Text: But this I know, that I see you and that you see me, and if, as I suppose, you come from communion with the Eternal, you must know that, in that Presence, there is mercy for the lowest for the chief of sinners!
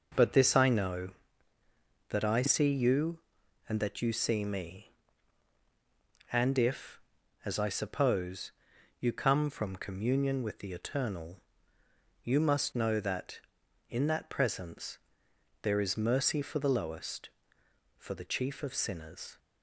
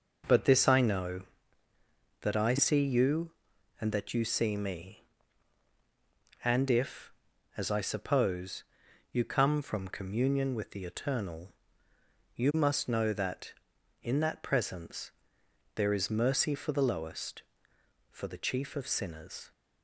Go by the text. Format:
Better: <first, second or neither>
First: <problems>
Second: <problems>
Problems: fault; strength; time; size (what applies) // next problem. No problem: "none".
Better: neither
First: none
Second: none